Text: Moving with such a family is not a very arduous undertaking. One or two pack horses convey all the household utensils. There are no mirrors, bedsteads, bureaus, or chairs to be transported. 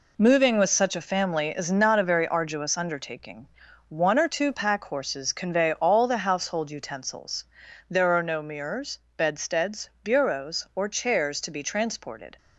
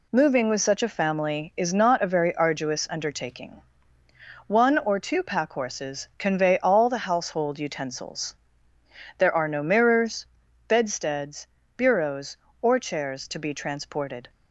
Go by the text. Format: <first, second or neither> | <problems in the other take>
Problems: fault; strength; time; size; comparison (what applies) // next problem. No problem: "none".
neither | none